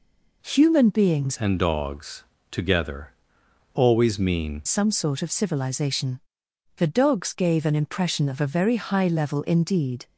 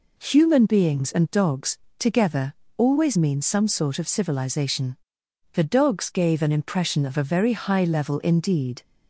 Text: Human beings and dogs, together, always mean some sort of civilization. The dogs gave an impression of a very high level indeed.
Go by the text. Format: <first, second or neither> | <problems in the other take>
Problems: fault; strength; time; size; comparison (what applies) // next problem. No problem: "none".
second | changes voice from "and" to "mean"; from 1.3 to 4.6 s; 3.3 s long